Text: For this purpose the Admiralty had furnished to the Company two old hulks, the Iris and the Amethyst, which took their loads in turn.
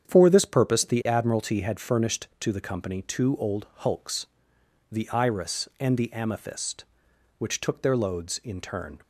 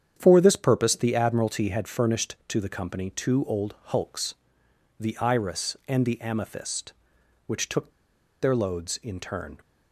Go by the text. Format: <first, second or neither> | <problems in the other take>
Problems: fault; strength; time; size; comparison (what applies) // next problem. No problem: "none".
first | starts louder than the rest; strong; until 1.1 s; 8.5 dB; strong in the first // pauses between "took" and "their"; noticeable; at 7.9 s; 0.51 s long